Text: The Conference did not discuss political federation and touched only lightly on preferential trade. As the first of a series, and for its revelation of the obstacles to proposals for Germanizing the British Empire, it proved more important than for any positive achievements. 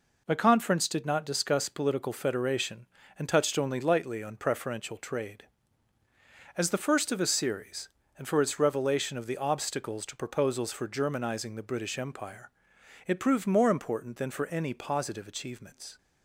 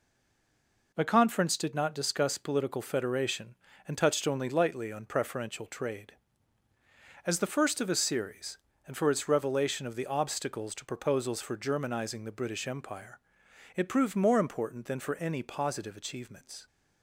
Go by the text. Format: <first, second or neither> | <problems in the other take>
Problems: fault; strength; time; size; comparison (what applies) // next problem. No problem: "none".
first | stays silent before the first word; slight; until 0.9 s; 0.9 s long